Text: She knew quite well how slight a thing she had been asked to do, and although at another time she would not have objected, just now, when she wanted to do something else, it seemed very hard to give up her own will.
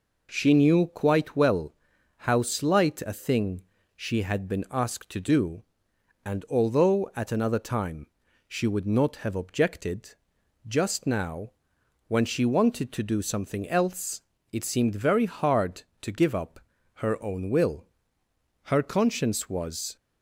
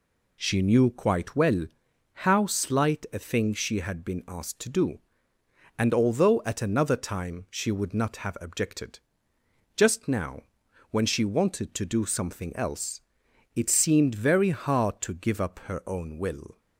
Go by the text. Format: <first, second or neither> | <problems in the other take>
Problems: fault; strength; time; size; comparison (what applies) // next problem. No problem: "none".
second | pauses between "well" and "how"; at 1.7 s; 0.44 s long; noticeable in the second // pauses between "thing" and "she"; slight; at 3.6 s; 0.32 s long // pauses between "time" and "she"; at 8.0 s; 0.42 s long // pauses between "up" and "her"; at 16.5 s; 0.42 s long // goes on to say "Her conscience was"; from 18.6 s on; 1.3 s long